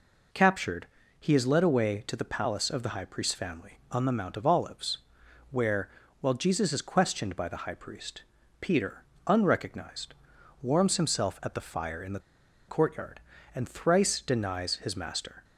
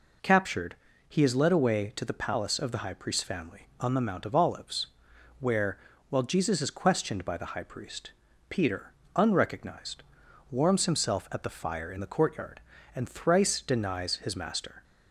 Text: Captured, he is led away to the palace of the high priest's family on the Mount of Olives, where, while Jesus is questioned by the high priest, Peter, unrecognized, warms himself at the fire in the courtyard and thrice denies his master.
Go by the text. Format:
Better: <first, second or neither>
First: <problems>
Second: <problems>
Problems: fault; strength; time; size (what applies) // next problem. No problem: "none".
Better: second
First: pauses between "the" and "courtyard"; noticeable; at 12.1 s; 0.49 s long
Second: none